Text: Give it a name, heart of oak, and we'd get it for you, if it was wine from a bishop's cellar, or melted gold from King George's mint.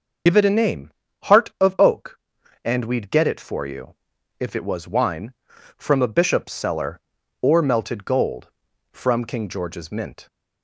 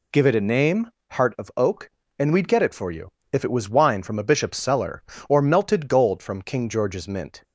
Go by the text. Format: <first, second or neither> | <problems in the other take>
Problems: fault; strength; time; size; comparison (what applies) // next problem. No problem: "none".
second | loses the start of "Give"; at 0.2 s; 45 ms // starts louder than the rest; until 1.6 s; 6.5 dB